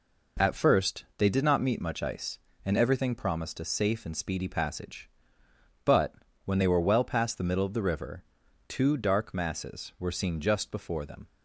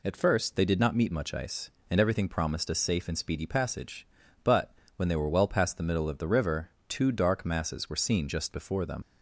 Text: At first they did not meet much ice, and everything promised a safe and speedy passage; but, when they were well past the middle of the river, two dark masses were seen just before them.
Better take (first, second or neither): first